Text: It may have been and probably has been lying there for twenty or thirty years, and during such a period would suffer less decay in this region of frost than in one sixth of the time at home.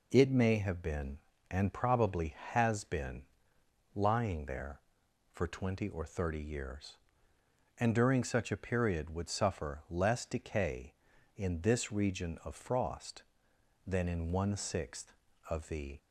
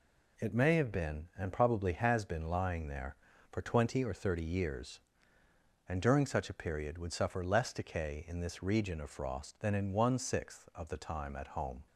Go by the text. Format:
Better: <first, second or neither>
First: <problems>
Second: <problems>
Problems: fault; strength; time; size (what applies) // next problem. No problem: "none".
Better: second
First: pauses between "been" and "lying"; noticeable; at 3.2 s; 0.72 s long // stops before "time at home"; at 15.9 s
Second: none